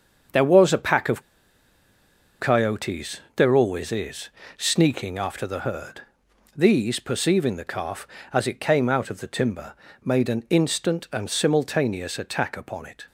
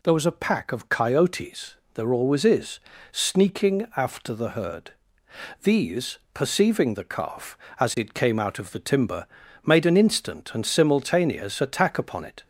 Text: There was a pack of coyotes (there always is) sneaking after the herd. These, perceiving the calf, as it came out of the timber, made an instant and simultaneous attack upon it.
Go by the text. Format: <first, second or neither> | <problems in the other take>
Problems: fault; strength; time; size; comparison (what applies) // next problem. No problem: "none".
second | starts louder than the rest; until 2.4 s; 6.5 dB // pauses between "of" and "coyotes"; at 1.2 s; 1.1 s long